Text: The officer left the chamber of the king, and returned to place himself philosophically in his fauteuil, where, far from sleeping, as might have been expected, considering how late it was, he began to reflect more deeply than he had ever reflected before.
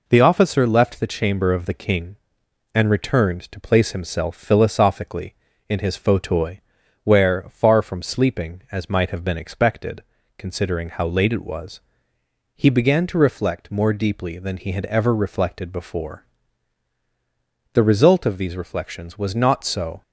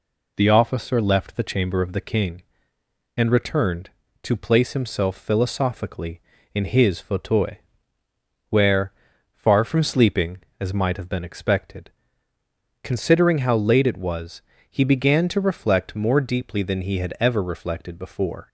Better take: second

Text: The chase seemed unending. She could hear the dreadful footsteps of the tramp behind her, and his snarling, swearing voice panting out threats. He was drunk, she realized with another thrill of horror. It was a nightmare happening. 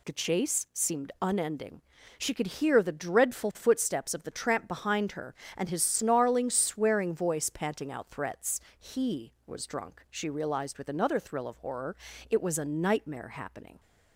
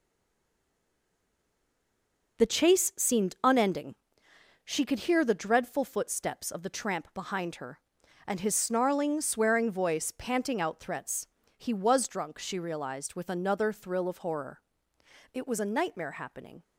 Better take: first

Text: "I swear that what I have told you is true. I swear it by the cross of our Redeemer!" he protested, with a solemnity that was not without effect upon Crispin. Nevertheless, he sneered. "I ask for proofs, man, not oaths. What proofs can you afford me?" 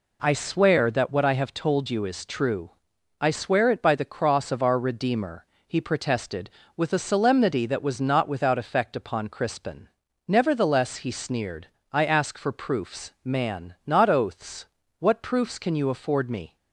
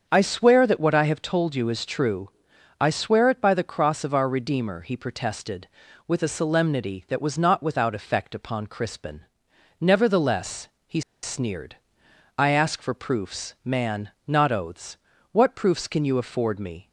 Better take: first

